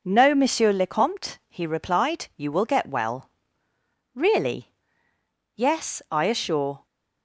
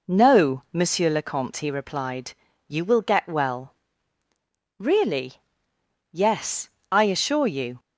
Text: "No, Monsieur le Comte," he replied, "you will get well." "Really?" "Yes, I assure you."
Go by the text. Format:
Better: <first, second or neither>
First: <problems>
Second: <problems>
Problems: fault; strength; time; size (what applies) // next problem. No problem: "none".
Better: second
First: stops before "you"; at 6.8 s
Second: none